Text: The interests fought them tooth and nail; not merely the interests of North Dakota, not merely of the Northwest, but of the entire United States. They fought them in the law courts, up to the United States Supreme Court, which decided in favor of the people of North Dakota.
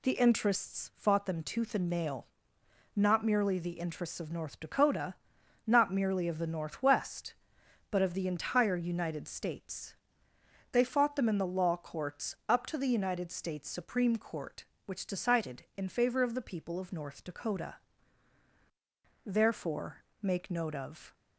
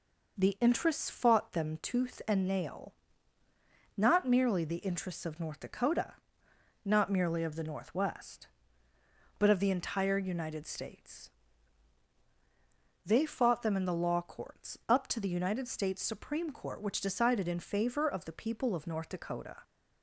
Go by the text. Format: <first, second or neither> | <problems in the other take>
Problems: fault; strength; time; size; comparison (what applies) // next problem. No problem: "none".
second | goes on to say "Therefore make note of"; strong; from 19.2 s on; 1.8 s long